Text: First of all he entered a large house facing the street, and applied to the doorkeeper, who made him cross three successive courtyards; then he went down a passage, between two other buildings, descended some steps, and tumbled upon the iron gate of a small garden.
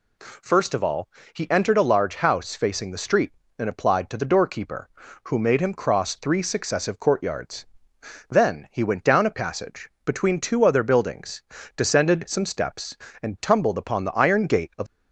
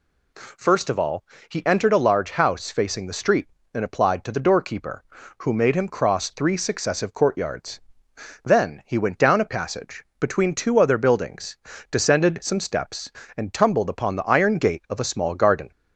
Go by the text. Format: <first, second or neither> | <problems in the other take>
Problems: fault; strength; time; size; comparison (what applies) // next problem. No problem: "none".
second | pauses between "all" and "he"; slight; at 1.0 s; 0.26 s long; slight in the second // stops before "a small garden"; at 14.8 s